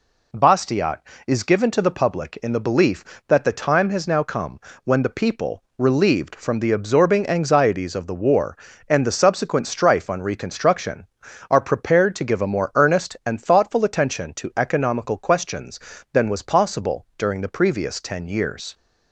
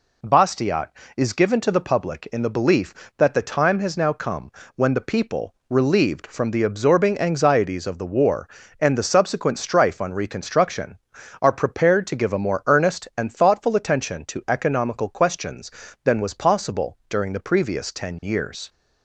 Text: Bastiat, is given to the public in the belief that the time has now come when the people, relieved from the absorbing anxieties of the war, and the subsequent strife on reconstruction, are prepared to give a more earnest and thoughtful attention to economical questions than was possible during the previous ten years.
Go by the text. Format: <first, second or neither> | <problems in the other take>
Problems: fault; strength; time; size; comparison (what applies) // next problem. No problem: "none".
neither | pauses between "come" and "when"; slight; the same in both